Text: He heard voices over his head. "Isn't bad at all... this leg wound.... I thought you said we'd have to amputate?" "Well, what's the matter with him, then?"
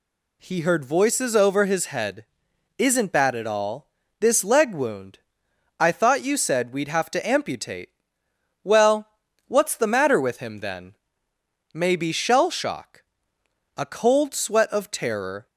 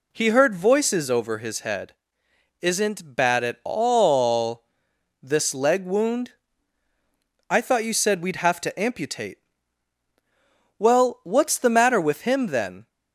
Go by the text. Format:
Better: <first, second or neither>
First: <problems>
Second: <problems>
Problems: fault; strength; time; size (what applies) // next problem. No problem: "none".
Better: second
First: goes on to say "Maybe shell shock A cold sweat of terror"; strong; from 11.7 s on; 3.7 s long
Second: none